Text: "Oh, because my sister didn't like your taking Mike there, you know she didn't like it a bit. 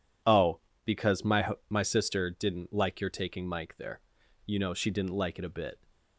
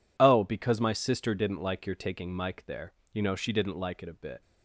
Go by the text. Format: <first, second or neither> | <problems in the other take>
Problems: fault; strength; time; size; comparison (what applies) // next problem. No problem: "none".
second | says "my" twice; at 1.6 s